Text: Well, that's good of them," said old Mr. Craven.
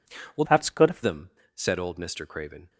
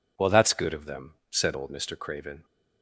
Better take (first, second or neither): second